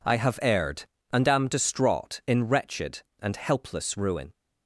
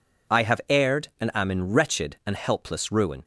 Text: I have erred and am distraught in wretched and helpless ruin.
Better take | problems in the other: first | skips "distraught"; at 1.4 s

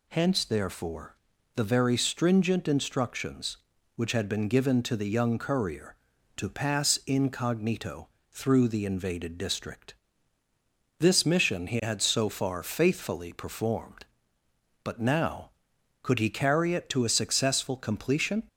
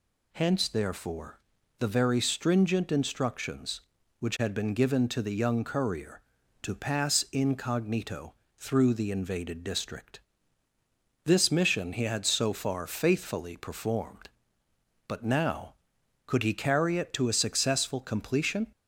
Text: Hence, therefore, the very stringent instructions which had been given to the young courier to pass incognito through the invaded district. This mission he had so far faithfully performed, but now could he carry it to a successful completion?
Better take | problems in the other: neither | pauses between "incognito" and "through"; slight; the same in both

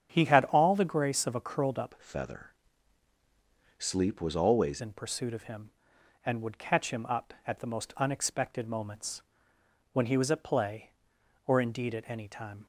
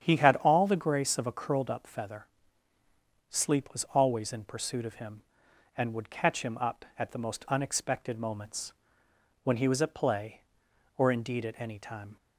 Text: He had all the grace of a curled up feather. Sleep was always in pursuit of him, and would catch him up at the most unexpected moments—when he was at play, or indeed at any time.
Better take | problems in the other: second | starts louder than the rest; strong; until 1.1 s; 8.5 dB; strong in the second // changes voice from "feather" to "always"; from 1.9 to 4.8 s; 2.9 s long

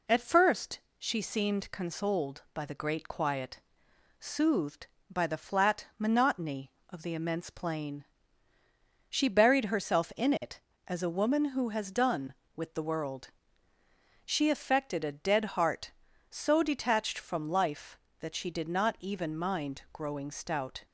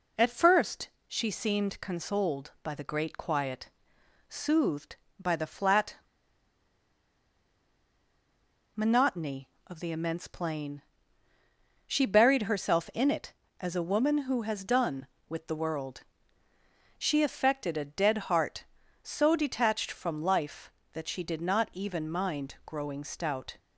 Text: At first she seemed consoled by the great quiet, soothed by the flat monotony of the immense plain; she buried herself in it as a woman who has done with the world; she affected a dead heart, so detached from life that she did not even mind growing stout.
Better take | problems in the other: first | pauses between "first" and "she"; slight; at 0.8 s; 0.18 s long; slight in the first // pauses between "flat" and "monotony"; strong; at 5.9 s; 2.8 s long

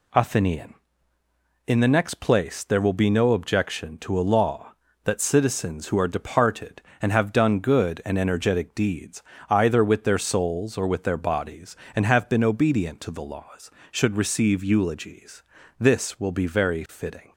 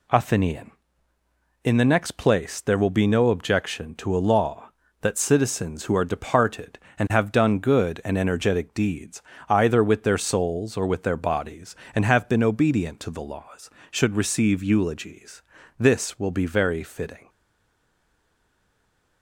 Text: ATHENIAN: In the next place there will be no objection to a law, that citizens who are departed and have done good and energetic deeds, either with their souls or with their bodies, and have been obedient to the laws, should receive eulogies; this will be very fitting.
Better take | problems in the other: first | stays silent after the last word; noticeable; from 17.2 s on; 2.0 s long

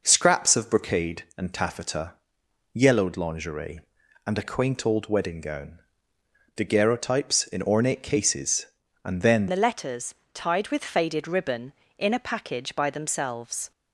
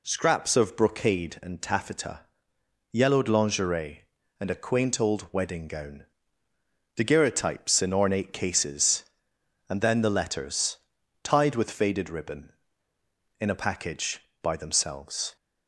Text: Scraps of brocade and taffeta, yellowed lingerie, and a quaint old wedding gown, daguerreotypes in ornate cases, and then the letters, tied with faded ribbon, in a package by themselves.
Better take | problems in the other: second | changes voice at "the"; from 9.4 s on; 4.3 s long

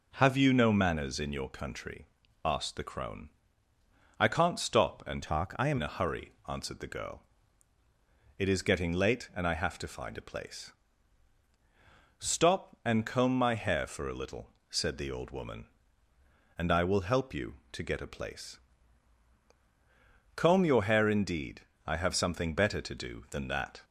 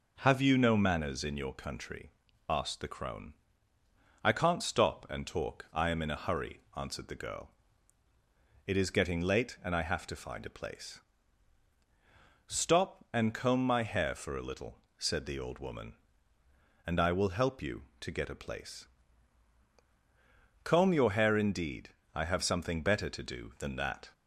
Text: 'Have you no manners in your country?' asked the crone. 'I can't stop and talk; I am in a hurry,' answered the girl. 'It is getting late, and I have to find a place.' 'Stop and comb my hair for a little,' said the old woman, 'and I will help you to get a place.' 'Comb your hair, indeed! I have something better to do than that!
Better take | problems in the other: second | changes voice from "talk" to "am"; from 5.2 to 5.7 s; 0.5 s long

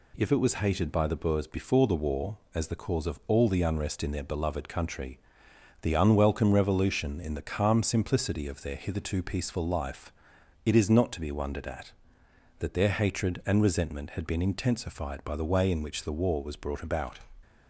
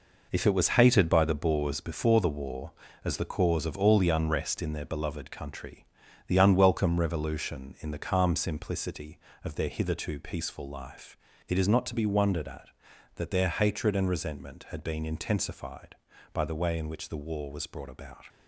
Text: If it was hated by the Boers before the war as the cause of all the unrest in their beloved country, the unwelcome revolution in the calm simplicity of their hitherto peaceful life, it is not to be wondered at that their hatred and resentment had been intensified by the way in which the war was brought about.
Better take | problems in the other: first | gets quieter; strong; throughout; 8.5 dB

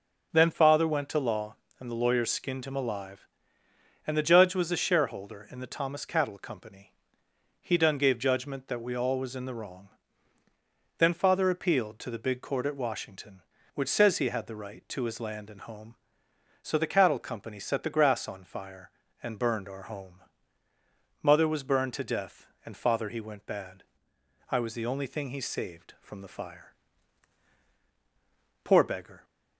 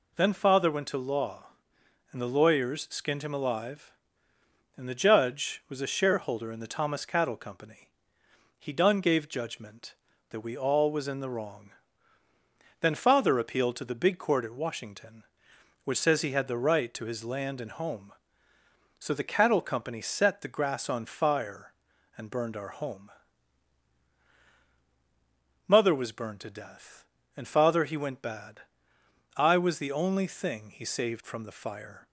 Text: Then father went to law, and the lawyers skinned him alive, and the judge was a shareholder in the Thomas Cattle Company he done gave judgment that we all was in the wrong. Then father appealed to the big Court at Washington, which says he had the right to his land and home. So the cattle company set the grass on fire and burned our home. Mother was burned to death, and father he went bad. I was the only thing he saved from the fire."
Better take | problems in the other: second | starts louder than the rest; noticeable; until 1.3 s; 6 dB // pauses between "Company" and "he"; noticeable; at 6.9 s; 0.68 s long; noticeable in the second // goes on to say "Poor beggar"; from 28.6 s on; 0.60 s long

